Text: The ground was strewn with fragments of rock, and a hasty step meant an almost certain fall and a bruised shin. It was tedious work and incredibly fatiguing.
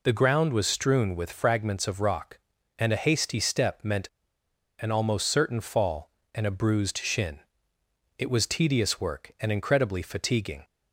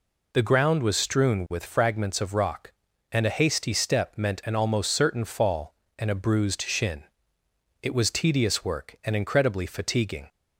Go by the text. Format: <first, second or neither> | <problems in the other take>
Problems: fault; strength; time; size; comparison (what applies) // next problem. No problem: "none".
second | pauses between "meant" and "an"; noticeable; at 4.0 s; 0.75 s long